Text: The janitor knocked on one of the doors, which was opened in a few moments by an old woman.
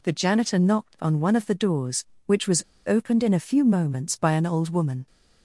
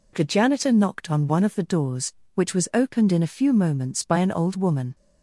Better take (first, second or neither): second